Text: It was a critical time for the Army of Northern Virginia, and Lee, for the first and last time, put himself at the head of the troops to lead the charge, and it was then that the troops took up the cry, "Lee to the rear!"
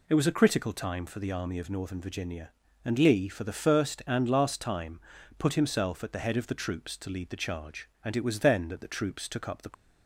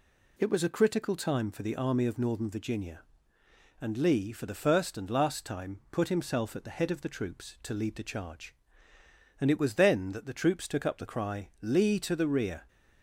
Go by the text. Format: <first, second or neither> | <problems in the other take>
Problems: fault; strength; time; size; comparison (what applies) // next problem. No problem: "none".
second | stops before "cry Lee to the rear"; at 9.7 s